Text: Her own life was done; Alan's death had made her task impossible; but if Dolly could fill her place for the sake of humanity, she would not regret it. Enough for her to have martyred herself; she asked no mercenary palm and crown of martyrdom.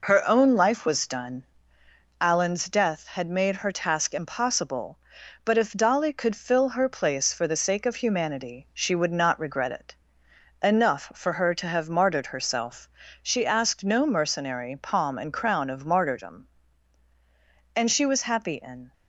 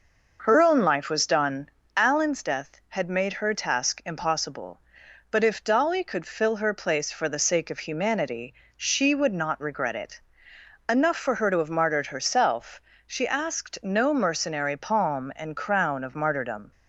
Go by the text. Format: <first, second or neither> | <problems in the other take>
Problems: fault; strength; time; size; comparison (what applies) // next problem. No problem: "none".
second | goes on to say "And she was happy in"; noticeable; from 17.7 s on; 1.1 s long